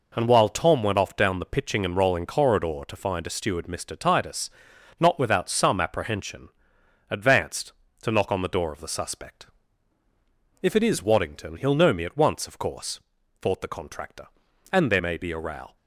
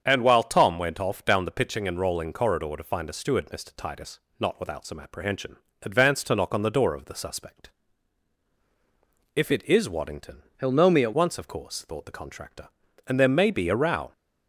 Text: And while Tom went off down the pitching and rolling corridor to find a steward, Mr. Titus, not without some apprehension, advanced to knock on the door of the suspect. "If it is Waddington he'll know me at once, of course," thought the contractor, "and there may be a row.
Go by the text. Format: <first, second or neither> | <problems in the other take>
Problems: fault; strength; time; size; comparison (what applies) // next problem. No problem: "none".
first | starts louder than the rest; strong; until 1.0 s; 7.5 dB // changes voice from "he'll" to "at"; from 10.6 to 11.1 s; 0.5 s long